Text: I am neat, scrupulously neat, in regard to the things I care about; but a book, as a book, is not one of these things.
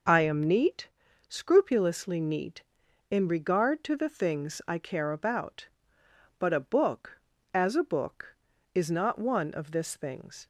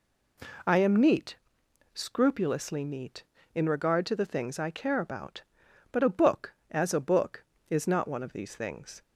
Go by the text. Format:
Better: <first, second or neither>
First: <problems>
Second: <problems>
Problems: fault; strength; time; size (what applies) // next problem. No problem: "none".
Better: second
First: says "this" for "these"; at 9.7 s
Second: none